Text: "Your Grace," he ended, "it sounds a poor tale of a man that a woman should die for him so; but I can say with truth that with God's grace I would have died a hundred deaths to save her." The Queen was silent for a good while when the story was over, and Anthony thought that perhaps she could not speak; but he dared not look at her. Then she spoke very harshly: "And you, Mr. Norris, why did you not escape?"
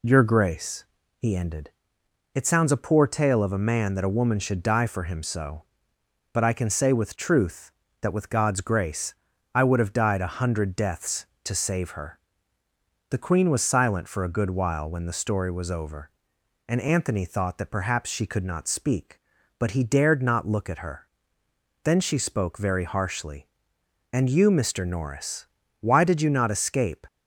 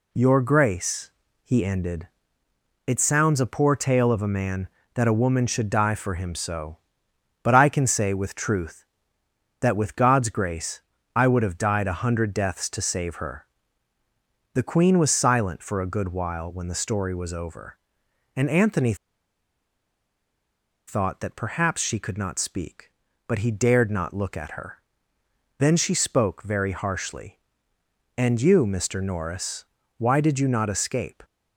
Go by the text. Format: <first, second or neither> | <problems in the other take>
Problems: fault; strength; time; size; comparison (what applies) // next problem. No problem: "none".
first | pauses between "grace" and "I"; slight; at 10.8 s; 0.34 s long; also in the first // pauses between "Anthony" and "thought"; strong; at 18.9 s; 1.9 s long